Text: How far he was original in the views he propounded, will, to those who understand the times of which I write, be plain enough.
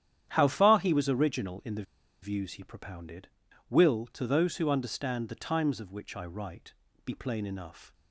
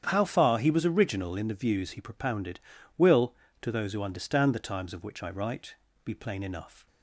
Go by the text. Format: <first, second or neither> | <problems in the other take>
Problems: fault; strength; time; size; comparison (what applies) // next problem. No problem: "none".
second | starts louder than the rest; strong; until 1.3 s; 10.5 dB; strong in the second // pauses between "the" and "views"; at 1.8 s; 0.39 s long